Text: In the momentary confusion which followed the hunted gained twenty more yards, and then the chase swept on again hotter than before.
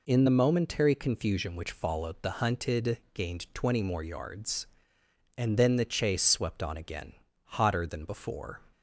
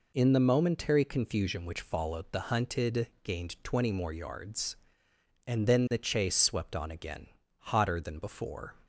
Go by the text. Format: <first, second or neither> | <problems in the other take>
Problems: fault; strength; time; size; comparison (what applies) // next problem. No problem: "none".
neither | pauses between "again" and "hotter"; slight; the same in both